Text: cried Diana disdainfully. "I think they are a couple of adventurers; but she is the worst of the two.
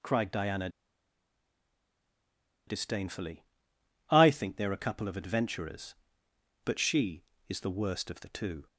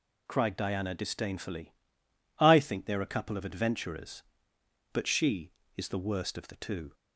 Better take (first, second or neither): second